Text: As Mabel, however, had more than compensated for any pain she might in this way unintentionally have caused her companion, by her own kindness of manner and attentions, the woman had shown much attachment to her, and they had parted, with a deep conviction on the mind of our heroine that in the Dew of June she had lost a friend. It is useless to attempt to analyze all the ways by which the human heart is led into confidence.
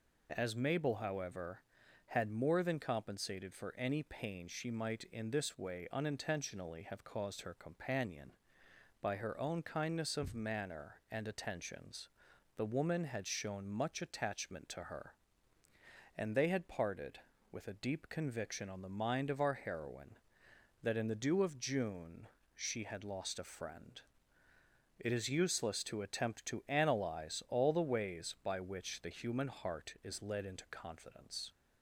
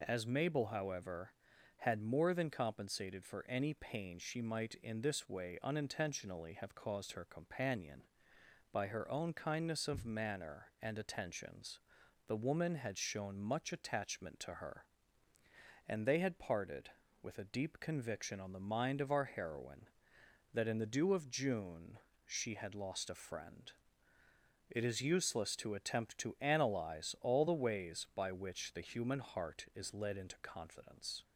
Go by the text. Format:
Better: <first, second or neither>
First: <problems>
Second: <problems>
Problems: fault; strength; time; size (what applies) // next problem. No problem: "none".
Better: neither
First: pauses between "June" and "she"; slight; at 22.2 s; 0.28 s long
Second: pauses between "June" and "she"; slight; at 21.9 s; 0.28 s long